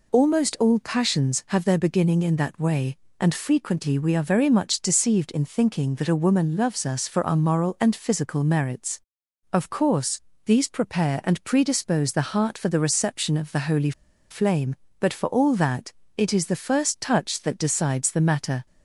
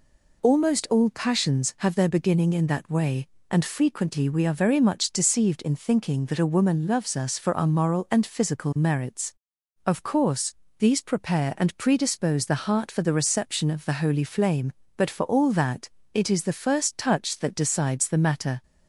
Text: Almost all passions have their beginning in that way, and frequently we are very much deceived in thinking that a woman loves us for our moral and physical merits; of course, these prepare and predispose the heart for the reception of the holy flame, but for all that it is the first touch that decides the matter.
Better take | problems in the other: second | pauses between "holy" and "flame"; at 13.9 s; 0.39 s long // pauses between "that" and "it"; slight; at 15.9 s; 0.22 s long; slight in the second

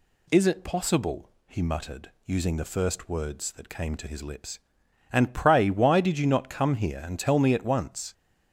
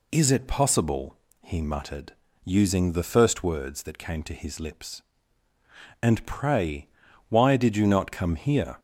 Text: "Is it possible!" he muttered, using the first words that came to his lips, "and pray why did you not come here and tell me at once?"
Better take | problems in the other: first | pauses between "pray" and "why"; at 6.8 s; 0.40 s long // stops before "and tell me at once"; at 8.7 s

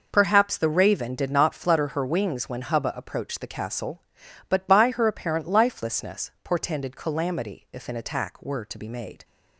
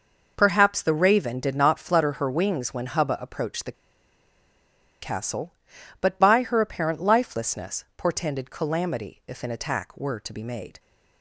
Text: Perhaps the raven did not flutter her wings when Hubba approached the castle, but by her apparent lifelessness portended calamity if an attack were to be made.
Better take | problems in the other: first | pauses between "the" and "castle"; strong; at 3.7 s; 1.2 s long

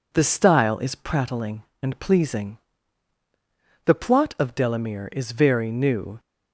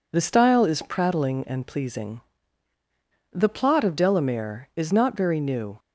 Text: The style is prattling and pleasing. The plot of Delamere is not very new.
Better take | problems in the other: second | skips "not"; at 5.3 s

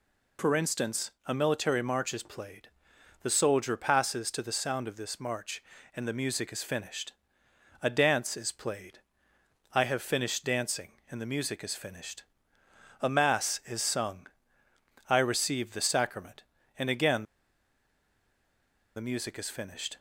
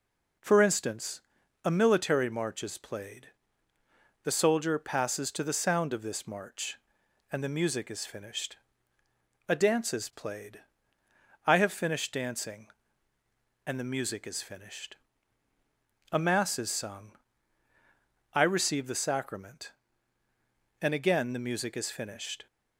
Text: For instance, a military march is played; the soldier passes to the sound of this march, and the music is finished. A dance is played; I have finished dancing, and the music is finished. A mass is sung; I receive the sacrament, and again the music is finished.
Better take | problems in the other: second | pauses between "again" and "the"; strong; at 17.2 s; 1.7 s long

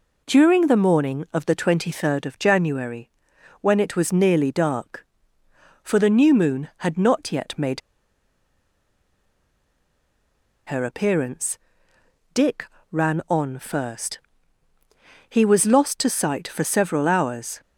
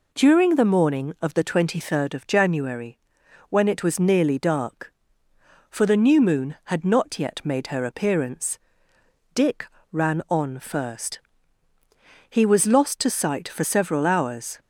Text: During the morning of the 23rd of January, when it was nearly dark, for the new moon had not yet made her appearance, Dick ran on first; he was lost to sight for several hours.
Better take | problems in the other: second | pauses between "made" and "her"; strong; at 7.8 s; 2.8 s long // pauses between "Dick" and "ran"; slight; at 12.6 s; 0.26 s long; slight in the second

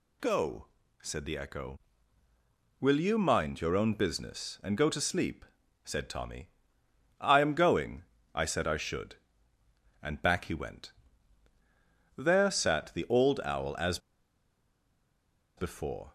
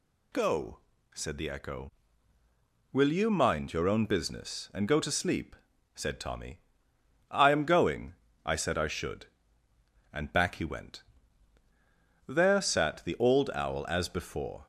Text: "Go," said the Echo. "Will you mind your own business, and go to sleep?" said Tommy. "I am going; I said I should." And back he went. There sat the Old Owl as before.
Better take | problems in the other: second | pauses between "as" and "before"; strong; at 13.9 s; 1.5 s long

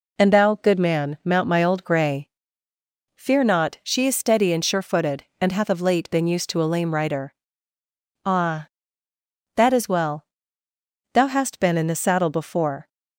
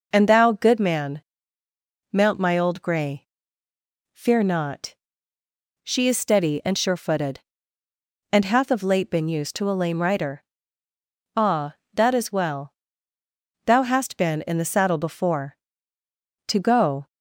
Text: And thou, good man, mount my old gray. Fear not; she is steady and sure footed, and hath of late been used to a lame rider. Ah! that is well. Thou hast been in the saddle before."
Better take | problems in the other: first | goes on to say "To go"; from 16.4 s on; 0.58 s long

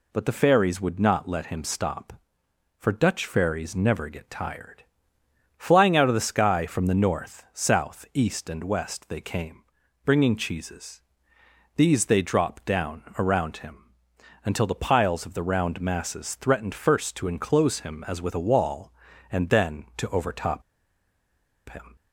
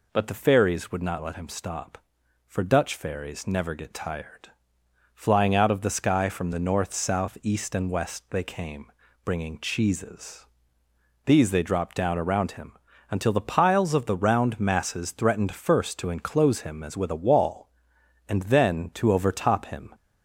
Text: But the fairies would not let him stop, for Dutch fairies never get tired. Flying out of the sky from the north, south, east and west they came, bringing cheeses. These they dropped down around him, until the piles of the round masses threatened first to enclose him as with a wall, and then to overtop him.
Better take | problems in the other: second | pauses between "down" and "around"; slight; at 13.0 s; 0.16 s long // pauses between "overtop" and "him"; at 20.6 s; 1.0 s long

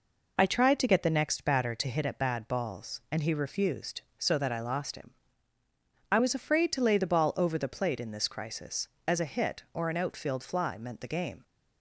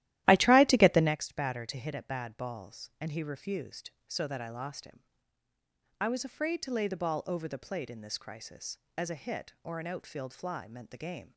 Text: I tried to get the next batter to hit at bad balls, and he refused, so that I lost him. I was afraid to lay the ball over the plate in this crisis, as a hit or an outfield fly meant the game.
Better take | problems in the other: first | starts louder than the rest; strong; until 1.1 s; 14 dB

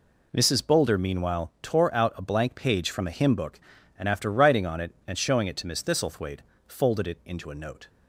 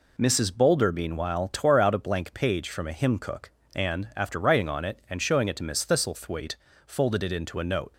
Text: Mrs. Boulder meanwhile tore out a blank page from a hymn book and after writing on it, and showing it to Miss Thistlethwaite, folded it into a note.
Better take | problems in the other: first | says "cook" for "book"; at 3.1 s

